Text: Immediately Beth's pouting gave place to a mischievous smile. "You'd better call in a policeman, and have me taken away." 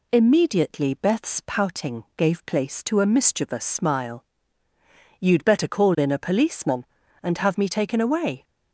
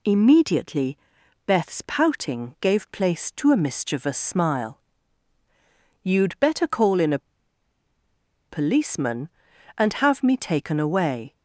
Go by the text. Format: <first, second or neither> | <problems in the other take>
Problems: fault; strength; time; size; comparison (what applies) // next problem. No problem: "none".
first | pauses between "Immediately" and "Beth's"; noticeable; at 0.9 s; 0.48 s long // pauses between "a" and "policeman"; strong; at 7.1 s; 1.2 s long